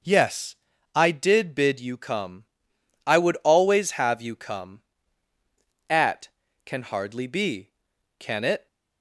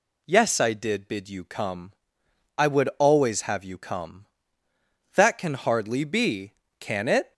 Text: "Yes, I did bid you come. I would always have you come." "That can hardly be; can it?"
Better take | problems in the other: second | says "At" for "That"; at 5.8 s

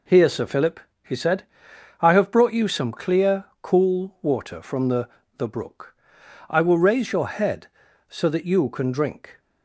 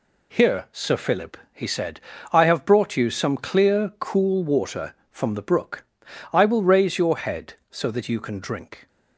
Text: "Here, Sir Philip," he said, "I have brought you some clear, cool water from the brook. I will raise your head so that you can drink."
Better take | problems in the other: second | says "the" twice; at 5.3 s

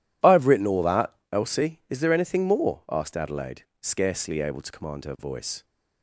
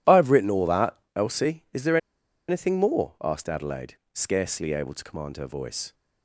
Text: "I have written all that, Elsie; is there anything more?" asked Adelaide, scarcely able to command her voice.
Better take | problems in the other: first | pauses between "there" and "anything"; noticeable; at 1.9 s; 0.51 s long

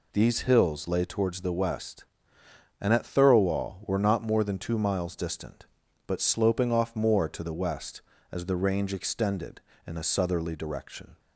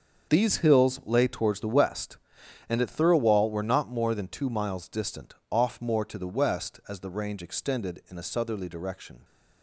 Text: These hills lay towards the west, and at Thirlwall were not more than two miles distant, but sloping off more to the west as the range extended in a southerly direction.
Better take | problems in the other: first | starts louder than the rest; until 1.3 s; 6.5 dB // skips "but sloping"; at 5.4 s

